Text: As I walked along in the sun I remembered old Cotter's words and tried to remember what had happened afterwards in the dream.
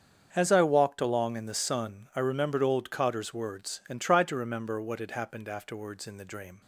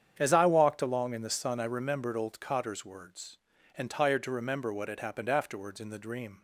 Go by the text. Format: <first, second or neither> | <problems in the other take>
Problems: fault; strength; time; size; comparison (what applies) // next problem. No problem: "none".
first | starts louder than the rest; strong; until 1.2 s; 8.5 dB; strong in the first // says "tired" for "tried"; at 3.8 s